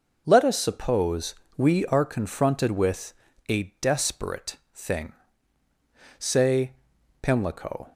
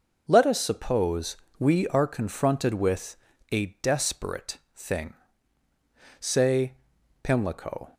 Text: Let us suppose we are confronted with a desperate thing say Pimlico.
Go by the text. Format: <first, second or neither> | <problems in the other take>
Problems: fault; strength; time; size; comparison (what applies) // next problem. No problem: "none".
neither | starts louder than the rest; noticeable; the same in both // pauses between "suppose" and "we"; slight; the same in both // pauses between "with" and "a"; slight; the same in both // pauses between "desperate" and "thing"; slight; the same in both // pauses between "thing" and "say"; the same in both // pauses between "say" and "Pimlico"; noticeable; the same in both